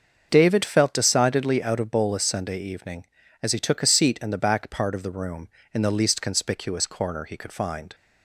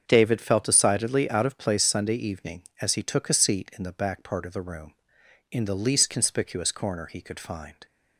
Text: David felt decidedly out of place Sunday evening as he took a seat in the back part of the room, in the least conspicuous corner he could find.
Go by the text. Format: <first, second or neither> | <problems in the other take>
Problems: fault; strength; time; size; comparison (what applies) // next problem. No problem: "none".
second | starts louder than the rest; until 1.3 s; 6.5 dB; also in the second // says "bolus" for "place"; at 1.8 s